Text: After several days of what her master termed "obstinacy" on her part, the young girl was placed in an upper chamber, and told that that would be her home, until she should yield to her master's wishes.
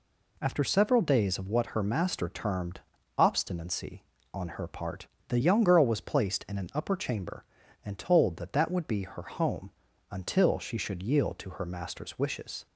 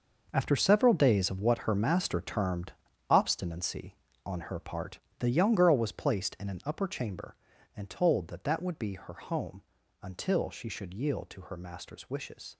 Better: first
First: pauses between "termed" and "obstinacy"; slight; at 2.8 s; 0.36 s long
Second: gets quieter; strong; throughout; 11.5 dB // pauses between "termed" and "obstinacy"; slight; at 2.7 s; 0.36 s long

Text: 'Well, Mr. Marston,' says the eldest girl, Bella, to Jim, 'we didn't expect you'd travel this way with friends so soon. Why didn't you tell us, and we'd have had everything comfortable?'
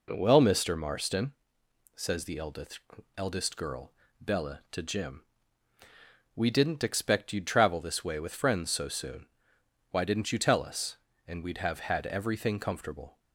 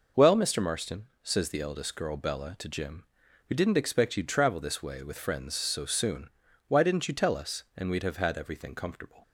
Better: second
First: says "eldest" twice; at 3.1 s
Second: none

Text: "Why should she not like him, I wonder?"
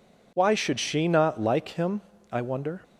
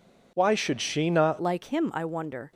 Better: first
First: none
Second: changes voice at "like"; from 1.3 s on; 1.2 s long

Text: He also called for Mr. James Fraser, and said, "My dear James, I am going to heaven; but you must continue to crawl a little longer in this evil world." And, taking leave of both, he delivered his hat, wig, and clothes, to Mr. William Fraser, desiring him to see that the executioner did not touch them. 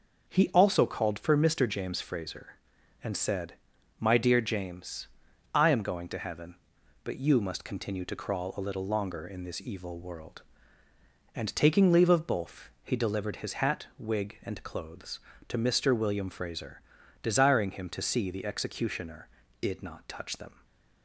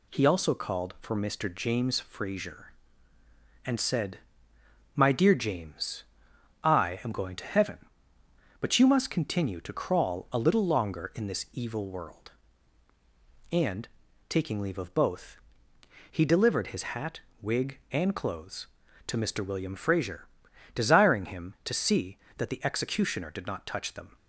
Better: second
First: skips "that"; at 18.2 s // stays silent after the last word; slight; from 20.5 s on; 0.5 s long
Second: none

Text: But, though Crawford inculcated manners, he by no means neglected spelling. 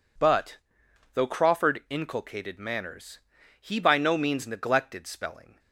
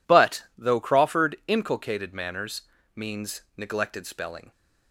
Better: first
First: none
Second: skips "he by no"; at 2.7 s

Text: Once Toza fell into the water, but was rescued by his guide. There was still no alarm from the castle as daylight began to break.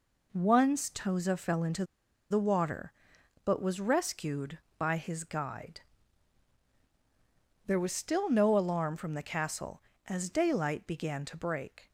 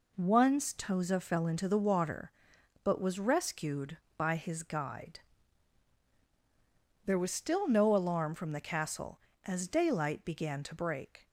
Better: second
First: pauses between "into" and "the"; noticeable; at 1.8 s; 0.46 s long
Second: none

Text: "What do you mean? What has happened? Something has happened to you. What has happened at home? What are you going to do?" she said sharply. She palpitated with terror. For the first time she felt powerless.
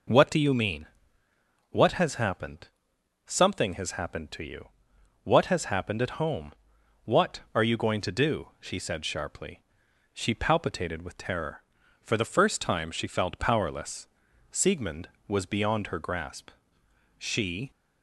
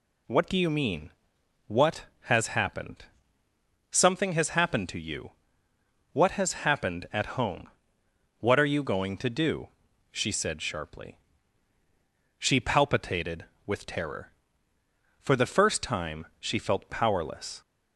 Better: second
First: goes on to say "Siegmund was beyond her grasp She"; strong; from 14.5 s on; 3.2 s long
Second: none

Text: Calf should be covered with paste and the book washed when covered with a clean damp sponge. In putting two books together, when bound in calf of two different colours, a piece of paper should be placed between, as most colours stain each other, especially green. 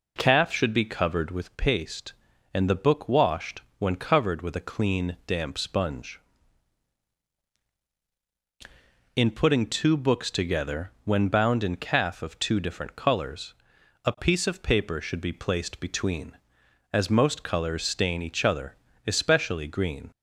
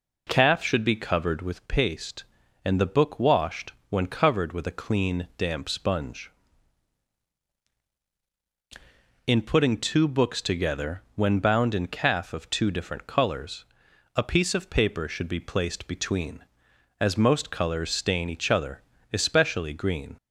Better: neither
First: pauses between "washed" and "when"; slight; at 3.6 s; 0.16 s long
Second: pauses between "washed" and "when"; slight; at 3.7 s; 0.16 s long

